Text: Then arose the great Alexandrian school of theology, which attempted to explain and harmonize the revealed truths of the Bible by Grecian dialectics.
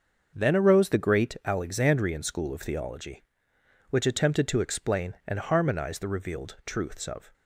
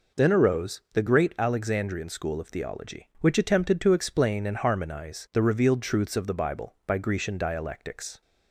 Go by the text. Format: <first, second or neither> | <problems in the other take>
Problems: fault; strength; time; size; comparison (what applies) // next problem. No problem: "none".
second | starts louder than the rest; until 1.3 s; 6 dB // stops before "the Bible by Grecian dialectics"; at 7.3 s